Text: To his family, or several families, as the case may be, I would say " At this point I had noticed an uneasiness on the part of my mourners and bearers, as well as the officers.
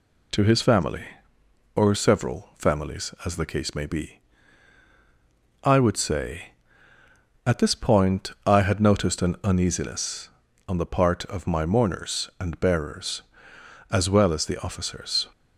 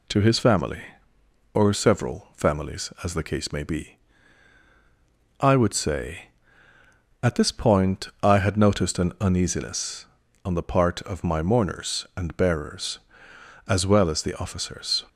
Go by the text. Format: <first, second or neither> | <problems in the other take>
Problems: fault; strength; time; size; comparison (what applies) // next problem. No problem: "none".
neither | none